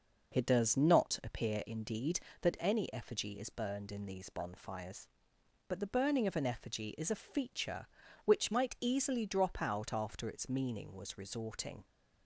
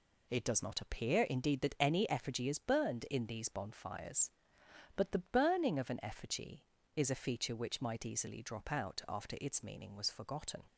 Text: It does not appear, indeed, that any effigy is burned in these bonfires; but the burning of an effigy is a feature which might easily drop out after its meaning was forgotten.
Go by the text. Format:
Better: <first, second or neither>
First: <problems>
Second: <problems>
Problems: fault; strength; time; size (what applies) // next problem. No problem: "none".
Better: second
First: says "resorting" for "forgotten"; at 11.1 s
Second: none